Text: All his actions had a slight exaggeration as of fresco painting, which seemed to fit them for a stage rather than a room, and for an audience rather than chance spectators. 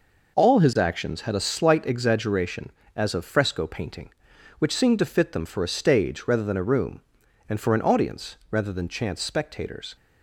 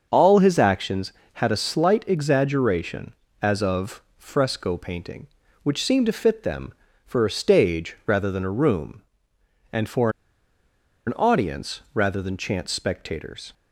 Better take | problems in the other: first | starts louder than the rest; until 1.1 s; 6.5 dB // pauses between "for" and "an"; noticeable; at 10.1 s; 0.96 s long

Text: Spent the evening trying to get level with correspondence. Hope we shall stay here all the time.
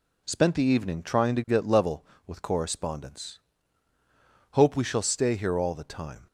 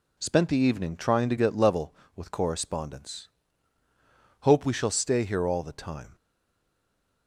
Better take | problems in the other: first | stays silent after the last word; from 6.1 s on; 1.1 s long

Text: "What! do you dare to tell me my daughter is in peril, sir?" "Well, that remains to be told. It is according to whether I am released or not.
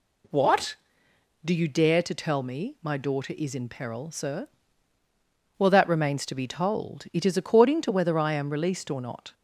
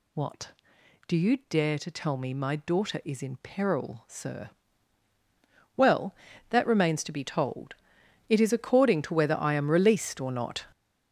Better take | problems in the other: first | gets louder; strong; throughout; 9 dB

